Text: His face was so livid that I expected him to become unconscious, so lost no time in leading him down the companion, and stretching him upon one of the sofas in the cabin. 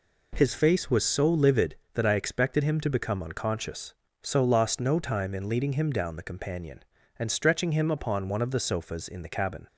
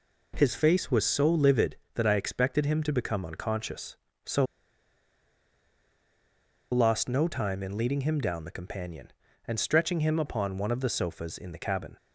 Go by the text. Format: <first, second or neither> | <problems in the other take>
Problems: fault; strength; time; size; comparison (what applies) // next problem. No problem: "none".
first | pauses between "so" and "lost"; strong; at 4.4 s; 2.2 s long